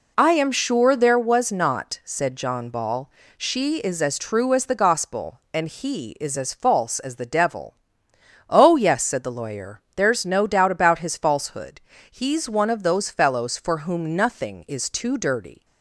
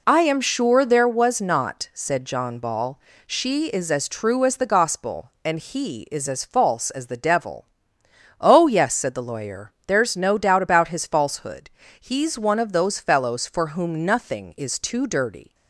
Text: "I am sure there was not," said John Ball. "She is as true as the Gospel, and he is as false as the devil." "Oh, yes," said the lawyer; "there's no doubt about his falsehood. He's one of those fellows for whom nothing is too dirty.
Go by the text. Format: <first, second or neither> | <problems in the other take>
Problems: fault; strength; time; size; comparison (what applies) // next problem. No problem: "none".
neither | none